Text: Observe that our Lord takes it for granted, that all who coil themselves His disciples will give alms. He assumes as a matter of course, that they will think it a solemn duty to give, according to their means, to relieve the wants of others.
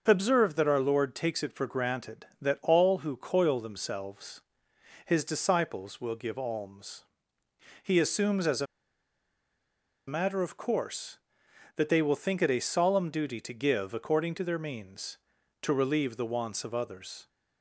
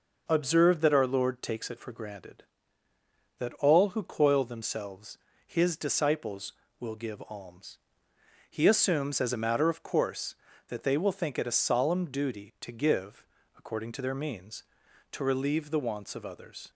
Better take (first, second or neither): second